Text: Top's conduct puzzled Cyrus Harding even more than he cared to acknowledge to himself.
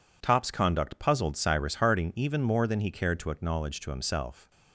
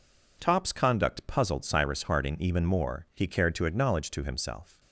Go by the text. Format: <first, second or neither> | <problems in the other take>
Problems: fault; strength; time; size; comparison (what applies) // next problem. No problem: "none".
first | skips "than"; at 3.0 s